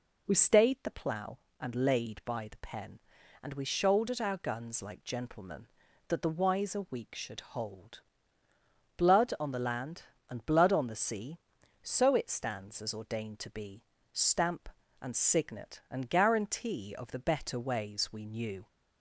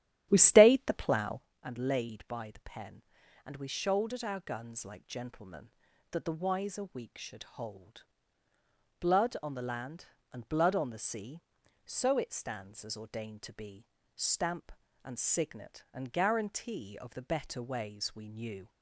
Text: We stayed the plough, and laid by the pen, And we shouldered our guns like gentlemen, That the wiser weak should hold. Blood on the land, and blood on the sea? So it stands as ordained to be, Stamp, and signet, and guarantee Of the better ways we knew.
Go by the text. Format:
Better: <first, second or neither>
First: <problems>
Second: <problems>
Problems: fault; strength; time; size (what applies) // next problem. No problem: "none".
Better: first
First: none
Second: starts louder than the rest; strong; until 1.5 s; 11 dB